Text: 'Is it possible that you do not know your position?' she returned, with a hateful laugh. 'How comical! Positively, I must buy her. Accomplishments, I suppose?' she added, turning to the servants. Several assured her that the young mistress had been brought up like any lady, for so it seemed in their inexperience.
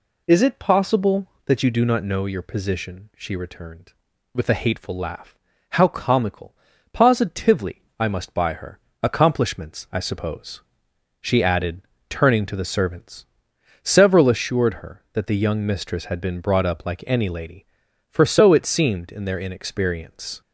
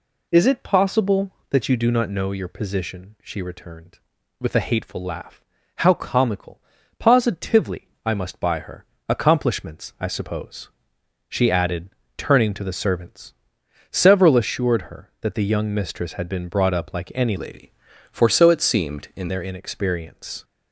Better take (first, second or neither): first